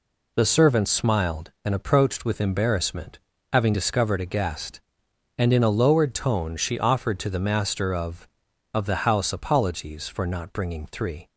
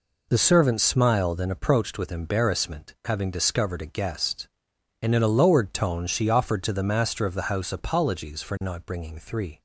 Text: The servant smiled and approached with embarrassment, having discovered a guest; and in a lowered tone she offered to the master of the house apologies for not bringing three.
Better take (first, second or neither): second